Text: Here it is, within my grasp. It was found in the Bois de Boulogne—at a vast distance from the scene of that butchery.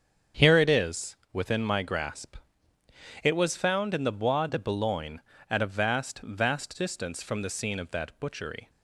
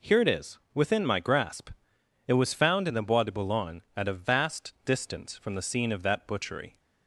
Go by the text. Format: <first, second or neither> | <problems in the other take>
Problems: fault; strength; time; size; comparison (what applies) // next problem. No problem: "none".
second | starts louder than the rest; strong; until 1.5 s; 7.5 dB // says "vast" twice; at 6.2 s